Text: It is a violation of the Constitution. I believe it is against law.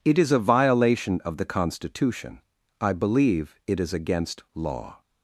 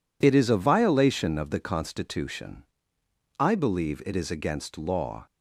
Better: neither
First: none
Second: none

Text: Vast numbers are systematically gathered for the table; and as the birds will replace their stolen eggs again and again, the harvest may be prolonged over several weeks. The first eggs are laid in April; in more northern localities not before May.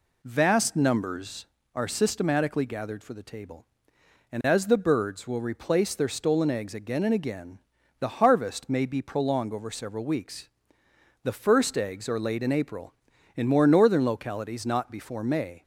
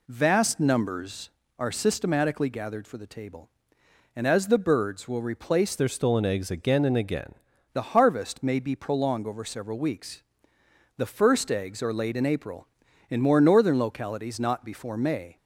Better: first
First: none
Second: changes voice from "their" to "again"; from 5.7 to 7.3 s; 1.6 s long

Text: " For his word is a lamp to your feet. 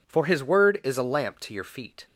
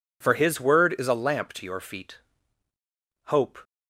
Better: first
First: none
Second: goes on to say "Hope"; slight; from 3.2 s on; 0.34 s long

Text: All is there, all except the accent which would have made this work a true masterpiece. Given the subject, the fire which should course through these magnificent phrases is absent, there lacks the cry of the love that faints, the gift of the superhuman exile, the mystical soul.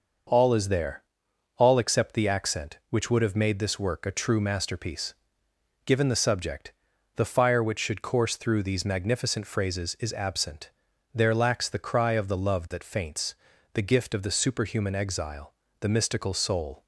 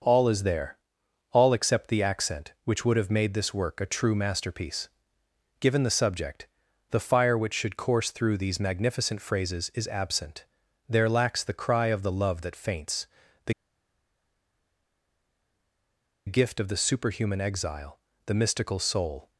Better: first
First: starts louder than the rest; noticeable; until 1.7 s; 6 dB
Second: starts louder than the rest; noticeable; until 1.5 s; 6 dB // pauses between "the" and "gift"; strong; at 13.5 s; 2.7 s long

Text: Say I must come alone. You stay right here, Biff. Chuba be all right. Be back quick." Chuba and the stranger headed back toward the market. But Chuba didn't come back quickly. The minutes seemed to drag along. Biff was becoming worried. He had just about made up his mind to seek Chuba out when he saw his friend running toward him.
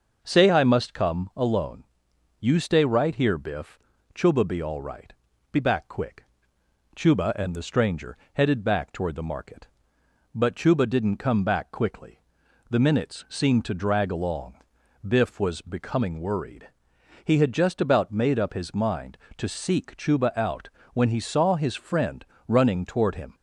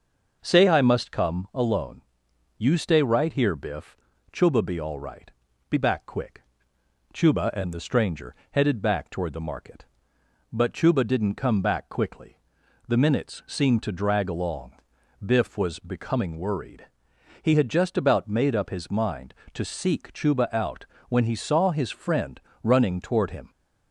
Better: neither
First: pauses between "stranger" and "headed"; slight; at 8.1 s; 0.18 s long // pauses between "out" and "when"; slight; at 20.6 s; 0.23 s long // pauses between "friend" and "running"; slight; at 22.2 s; 0.22 s long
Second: pauses between "stranger" and "headed"; slight; at 8.3 s; 0.18 s long // pauses between "out" and "when"; slight; at 20.8 s; 0.22 s long // pauses between "friend" and "running"; slight; at 22.3 s; 0.22 s long

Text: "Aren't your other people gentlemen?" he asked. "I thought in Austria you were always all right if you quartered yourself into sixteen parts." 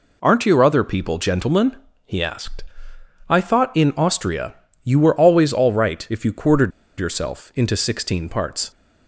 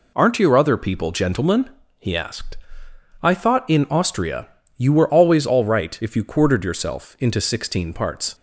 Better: second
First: pauses between "Austria" and "you"; slight; at 4.5 s; 0.30 s long // pauses between "quartered" and "yourself"; slight; at 6.7 s; 0.29 s long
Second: pauses between "Austria" and "you"; slight; at 4.4 s; 0.30 s long

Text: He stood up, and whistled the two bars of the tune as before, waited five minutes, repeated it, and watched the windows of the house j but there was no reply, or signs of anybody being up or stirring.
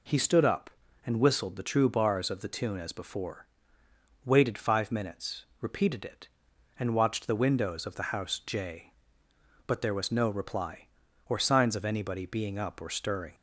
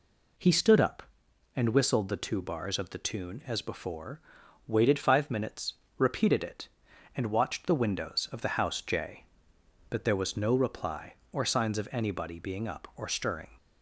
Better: second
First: says "true" for "two"; at 1.6 s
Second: none

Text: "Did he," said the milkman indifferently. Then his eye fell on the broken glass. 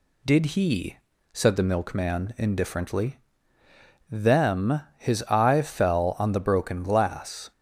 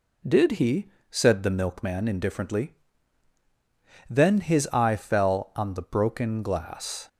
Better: second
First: says "Them" for "Then"; at 4.0 s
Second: none

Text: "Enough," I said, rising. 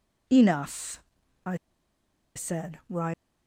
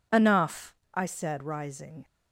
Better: second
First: pauses between "I" and "said"; noticeable; at 1.5 s; 0.80 s long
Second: none

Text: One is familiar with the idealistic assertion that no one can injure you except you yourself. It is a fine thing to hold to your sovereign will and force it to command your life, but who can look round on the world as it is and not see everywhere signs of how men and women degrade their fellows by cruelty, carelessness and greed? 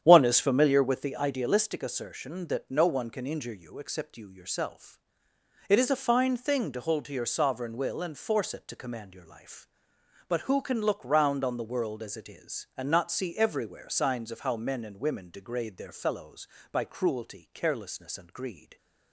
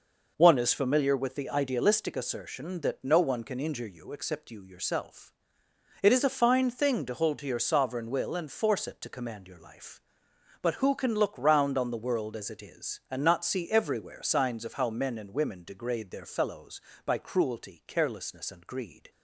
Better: second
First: starts louder than the rest; strong; until 1.2 s; 9.5 dB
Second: none

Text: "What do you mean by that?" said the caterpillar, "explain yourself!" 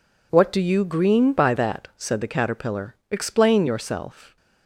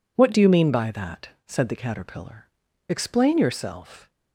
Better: second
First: says "green" for "mean"; at 0.8 s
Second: none

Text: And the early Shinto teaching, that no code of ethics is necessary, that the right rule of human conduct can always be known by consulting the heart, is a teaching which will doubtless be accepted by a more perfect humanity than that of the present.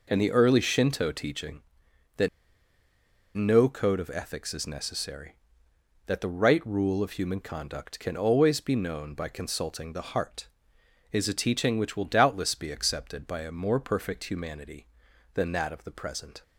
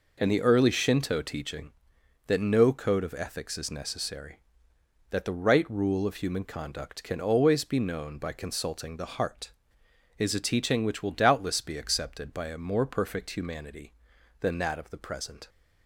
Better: second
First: pauses between "that" and "no"; at 2.2 s; 1.0 s long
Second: none

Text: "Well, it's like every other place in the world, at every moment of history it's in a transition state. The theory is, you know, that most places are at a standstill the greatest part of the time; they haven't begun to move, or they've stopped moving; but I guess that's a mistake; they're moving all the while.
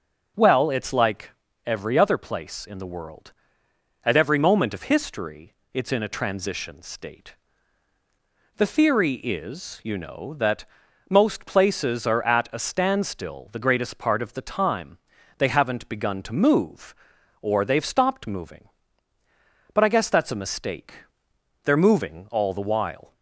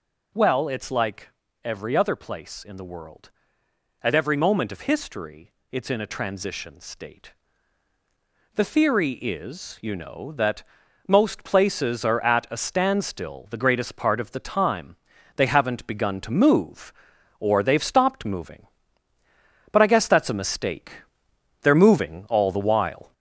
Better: first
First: pauses between "like" and "every"; slight; at 1.3 s; 0.36 s long // pauses between "history" and "it's"; slight; at 5.5 s; 0.18 s long // pauses between "that" and "most"; at 10.6 s; 0.44 s long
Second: gets louder; noticeable; throughout; 4.5 dB // pauses between "like" and "every"; slight; at 1.2 s; 0.36 s long // pauses between "history" and "it's"; slight; at 5.5 s; 0.18 s long // pauses between "that" and "most"; at 10.6 s; 0.44 s long

